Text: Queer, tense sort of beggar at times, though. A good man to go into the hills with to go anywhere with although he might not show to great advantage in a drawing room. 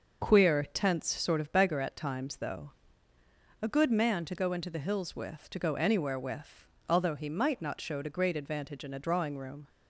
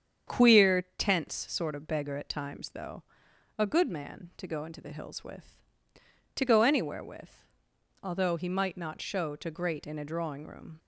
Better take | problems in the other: first | starts louder than the rest; strong; until 1.4 s; 8 dB // pauses between "with" and "although"; noticeable; at 7.4 s; 0.58 s long; slight in the first // skips "advantage"; at 9.8 s

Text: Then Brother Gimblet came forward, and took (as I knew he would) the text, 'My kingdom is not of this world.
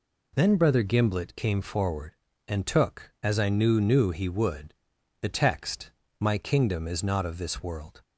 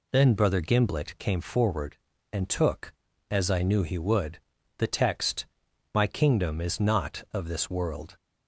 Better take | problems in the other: second | says "knew" twice; at 3.8 s

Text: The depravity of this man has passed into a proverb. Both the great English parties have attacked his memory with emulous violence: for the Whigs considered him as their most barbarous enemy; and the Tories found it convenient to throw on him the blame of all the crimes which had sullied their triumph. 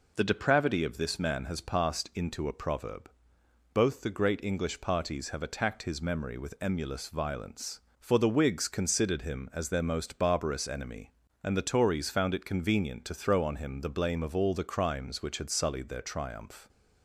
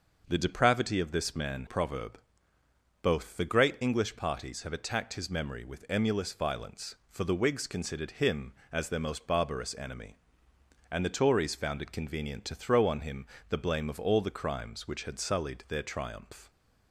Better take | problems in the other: first | skips "has passed into a"; at 1.6 s // pauses between "him" and "the"; slight; at 13.2 s; 0.22 s long

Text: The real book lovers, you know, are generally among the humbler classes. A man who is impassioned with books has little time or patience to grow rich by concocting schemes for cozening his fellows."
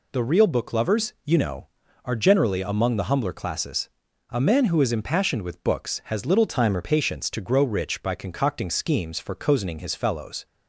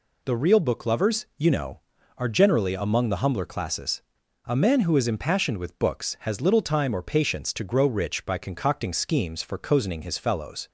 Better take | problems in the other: second | changes voice from "time" to "or"; from 6.4 to 6.8 s; 0.4 s long

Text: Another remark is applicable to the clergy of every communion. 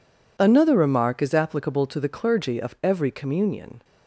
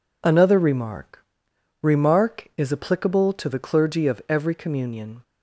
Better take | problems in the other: first | says "remark" twice; at 1.8 s

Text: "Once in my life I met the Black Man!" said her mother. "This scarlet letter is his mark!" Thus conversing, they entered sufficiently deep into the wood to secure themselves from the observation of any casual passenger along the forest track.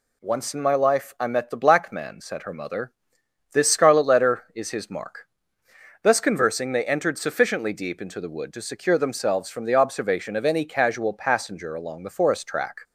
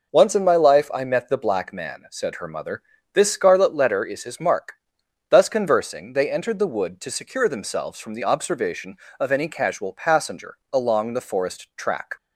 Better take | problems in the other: first | skips "sufficiently deep into"; at 6.5 s // pauses between "passenger" and "along"; slight; at 10.5 s; 0.16 s long

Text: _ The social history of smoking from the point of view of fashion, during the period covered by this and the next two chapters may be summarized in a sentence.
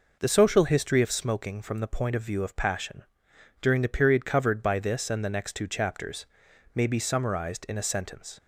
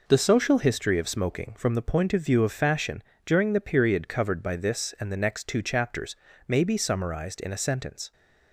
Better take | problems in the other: second | says "passion" for "fashion"; at 2.5 s // pauses between "chapters" and "may"; noticeable; at 6.2 s; 0.50 s long; slight in the second

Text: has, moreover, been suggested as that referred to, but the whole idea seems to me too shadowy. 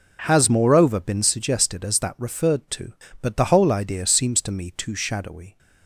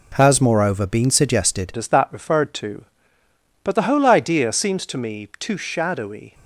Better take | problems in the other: first | changes voice at "as"; from 1.7 s on; 4.6 s long

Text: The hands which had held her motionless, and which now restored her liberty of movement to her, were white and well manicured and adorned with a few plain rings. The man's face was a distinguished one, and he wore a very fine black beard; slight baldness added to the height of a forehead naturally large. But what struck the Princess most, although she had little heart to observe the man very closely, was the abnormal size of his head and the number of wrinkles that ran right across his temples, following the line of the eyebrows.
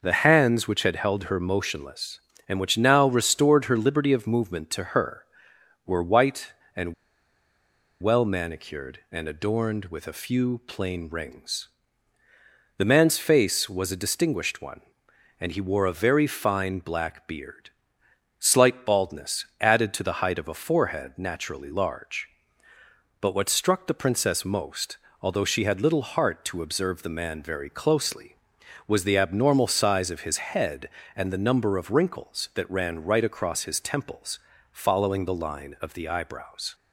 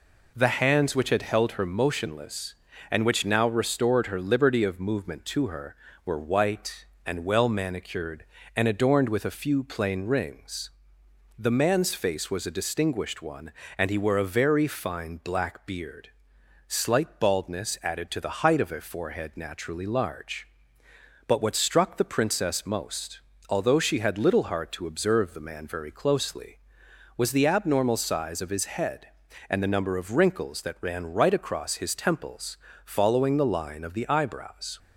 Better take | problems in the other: second | pauses between "and" and "well"; at 6.9 s; 1.0 s long

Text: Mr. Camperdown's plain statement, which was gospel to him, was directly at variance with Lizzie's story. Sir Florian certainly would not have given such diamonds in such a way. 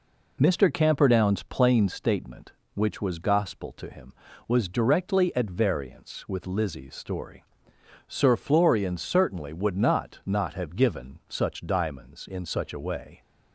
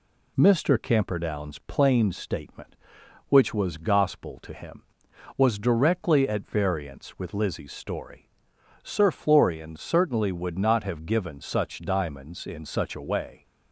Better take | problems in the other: second | says "not" twice; at 10.2 s

